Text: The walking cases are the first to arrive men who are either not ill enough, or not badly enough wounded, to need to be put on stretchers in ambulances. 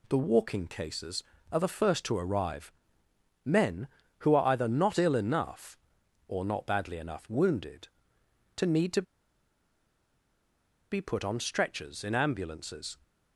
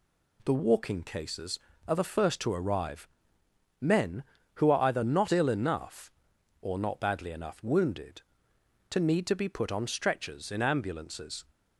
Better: second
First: pauses between "arrive" and "men"; noticeable; at 2.7 s; 0.72 s long // pauses between "to" and "be"; strong; at 9.0 s; 1.9 s long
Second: pauses between "arrive" and "men"; noticeable; at 3.0 s; 0.72 s long

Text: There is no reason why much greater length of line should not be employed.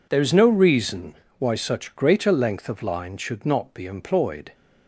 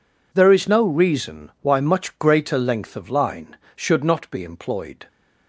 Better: second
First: pauses between "reason" and "why"; slight; at 1.1 s; 0.24 s long // says "such" for "much"; at 1.5 s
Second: none

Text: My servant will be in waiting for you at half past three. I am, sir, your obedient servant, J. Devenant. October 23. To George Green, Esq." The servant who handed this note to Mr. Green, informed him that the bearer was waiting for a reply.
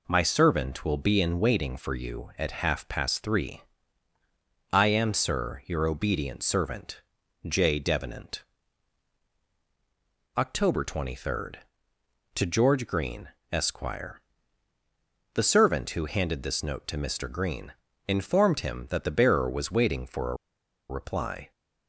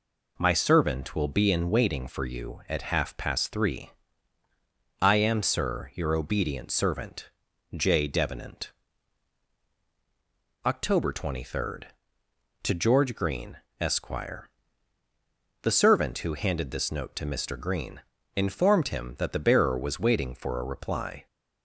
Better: second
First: pauses between "a" and "reply"; noticeable; at 20.3 s; 0.53 s long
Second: none

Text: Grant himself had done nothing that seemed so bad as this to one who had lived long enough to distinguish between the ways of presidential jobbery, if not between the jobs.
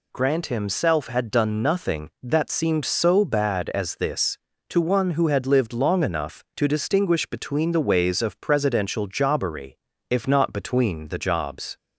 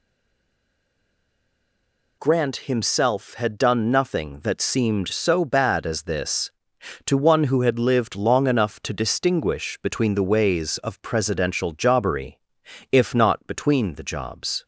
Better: first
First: none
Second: stays silent before the first word; until 2.2 s; 2.2 s long

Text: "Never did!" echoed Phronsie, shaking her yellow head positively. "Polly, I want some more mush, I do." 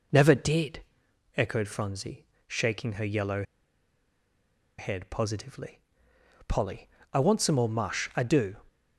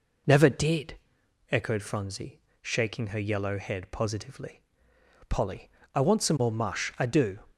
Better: second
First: pauses between "yellow" and "head"; strong; at 3.4 s; 1.3 s long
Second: none

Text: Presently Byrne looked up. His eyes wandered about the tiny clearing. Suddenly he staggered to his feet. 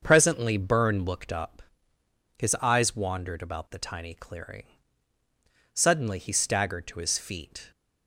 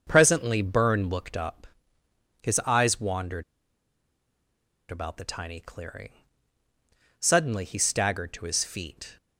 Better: first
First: starts louder than the rest; until 1.0 s; 6.5 dB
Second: starts louder than the rest; until 1.0 s; 6.5 dB // pauses between "wandered" and "about"; strong; at 3.4 s; 1.4 s long

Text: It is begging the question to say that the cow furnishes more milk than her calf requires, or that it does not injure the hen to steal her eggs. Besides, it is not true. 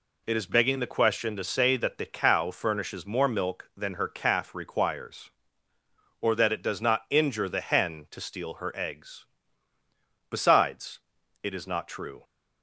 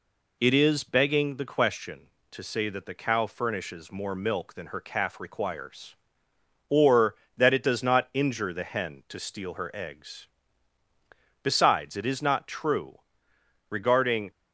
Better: first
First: none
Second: goes on to say "Regarding"; noticeable; from 13.6 s on; 0.62 s long

